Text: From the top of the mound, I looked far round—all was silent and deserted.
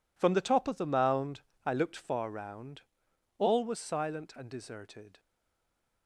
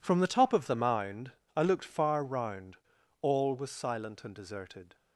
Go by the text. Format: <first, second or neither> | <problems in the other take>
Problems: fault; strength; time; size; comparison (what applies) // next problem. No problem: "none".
second | stays silent after the last word; slight; from 5.1 s on; 0.9 s long